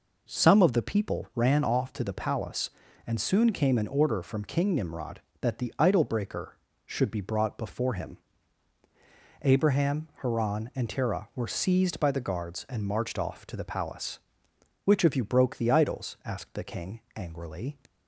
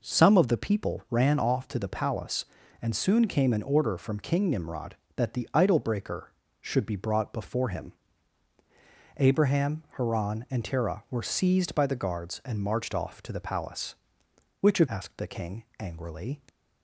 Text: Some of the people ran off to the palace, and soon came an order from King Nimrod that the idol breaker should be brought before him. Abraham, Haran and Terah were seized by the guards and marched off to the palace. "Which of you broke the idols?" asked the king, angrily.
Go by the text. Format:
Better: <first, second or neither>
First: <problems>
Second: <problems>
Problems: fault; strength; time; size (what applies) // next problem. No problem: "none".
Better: first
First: none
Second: skips "you broke the idols"; at 14.8 s